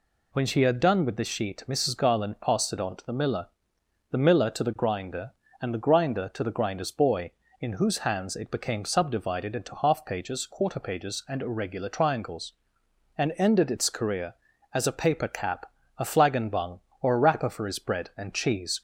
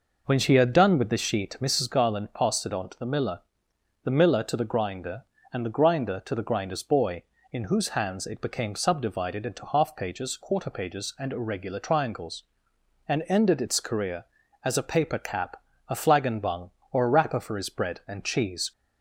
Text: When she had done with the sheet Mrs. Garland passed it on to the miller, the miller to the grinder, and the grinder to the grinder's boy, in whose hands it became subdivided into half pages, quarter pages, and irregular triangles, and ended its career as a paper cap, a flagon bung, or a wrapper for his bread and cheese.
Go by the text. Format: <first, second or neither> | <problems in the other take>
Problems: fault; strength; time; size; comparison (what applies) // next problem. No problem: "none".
first | starts louder than the rest; noticeable; until 1.9 s; 5.5 dB